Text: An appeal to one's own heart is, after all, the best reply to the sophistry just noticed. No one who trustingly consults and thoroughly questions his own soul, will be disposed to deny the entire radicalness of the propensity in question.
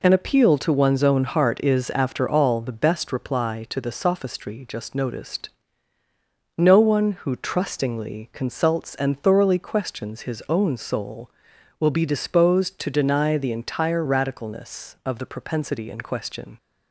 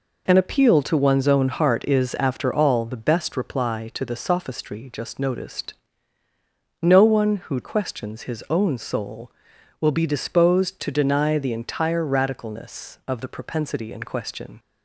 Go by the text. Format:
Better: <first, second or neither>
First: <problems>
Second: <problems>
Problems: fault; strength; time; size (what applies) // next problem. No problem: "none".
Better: first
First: none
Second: skips "trustingly consults and thoroughly"; at 7.6 s